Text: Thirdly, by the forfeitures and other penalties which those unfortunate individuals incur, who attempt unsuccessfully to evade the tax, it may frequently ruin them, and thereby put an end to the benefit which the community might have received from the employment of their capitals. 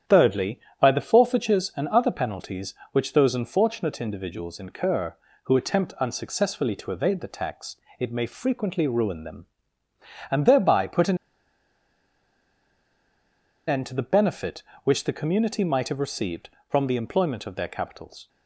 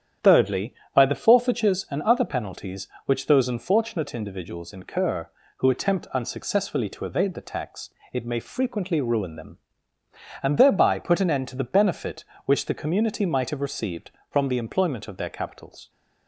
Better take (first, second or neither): second